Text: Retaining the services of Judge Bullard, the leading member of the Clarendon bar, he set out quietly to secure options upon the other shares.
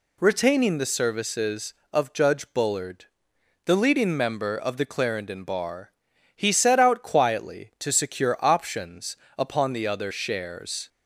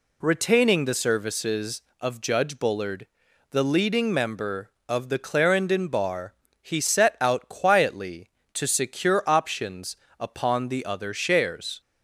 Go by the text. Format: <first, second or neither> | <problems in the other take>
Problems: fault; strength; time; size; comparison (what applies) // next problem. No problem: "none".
neither | pauses between "options" and "upon"; slight; the same in both